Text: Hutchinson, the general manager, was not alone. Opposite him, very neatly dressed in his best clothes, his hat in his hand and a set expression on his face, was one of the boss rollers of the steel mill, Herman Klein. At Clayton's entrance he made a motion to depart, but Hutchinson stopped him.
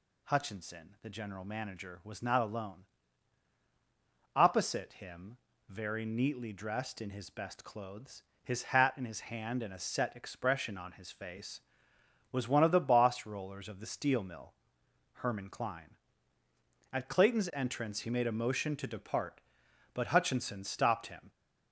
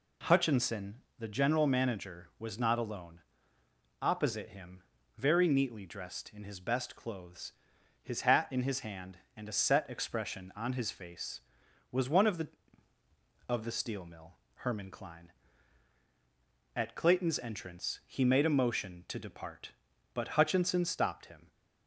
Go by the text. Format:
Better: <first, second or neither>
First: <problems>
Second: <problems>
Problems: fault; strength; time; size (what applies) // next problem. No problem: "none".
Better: first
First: none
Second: skips "boss rollers"; at 12.9 s